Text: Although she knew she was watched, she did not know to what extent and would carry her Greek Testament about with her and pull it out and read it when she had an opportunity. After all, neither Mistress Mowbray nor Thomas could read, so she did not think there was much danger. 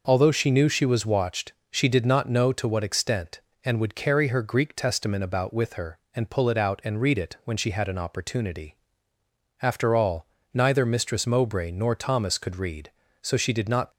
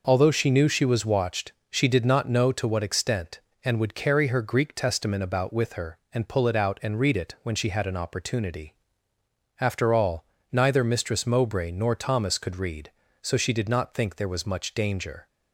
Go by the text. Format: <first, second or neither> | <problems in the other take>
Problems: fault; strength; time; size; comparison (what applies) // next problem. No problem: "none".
second | stops before "think there was much danger"; at 13.9 s